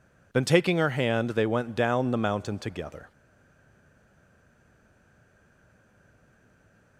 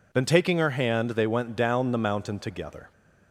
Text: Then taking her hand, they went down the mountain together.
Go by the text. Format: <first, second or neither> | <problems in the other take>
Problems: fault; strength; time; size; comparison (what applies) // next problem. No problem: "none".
second | stays silent after the last word; strong; from 3.1 s on; 3.8 s long